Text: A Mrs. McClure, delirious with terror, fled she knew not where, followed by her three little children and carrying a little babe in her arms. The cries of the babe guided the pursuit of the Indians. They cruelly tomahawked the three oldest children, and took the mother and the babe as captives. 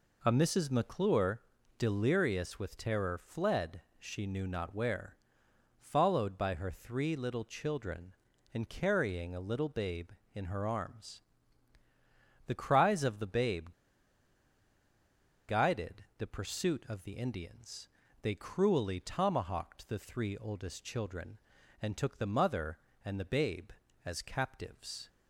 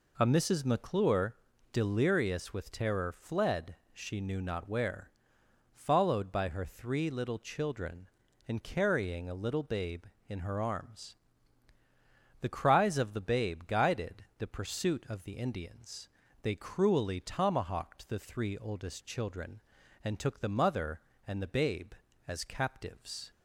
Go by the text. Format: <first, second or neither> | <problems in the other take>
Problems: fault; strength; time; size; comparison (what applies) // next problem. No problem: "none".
second | pauses between "fled" and "she"; slight; at 3.8 s; 0.16 s long; slight in the second // pauses between "babe" and "guided"; strong; at 13.6 s; 1.7 s long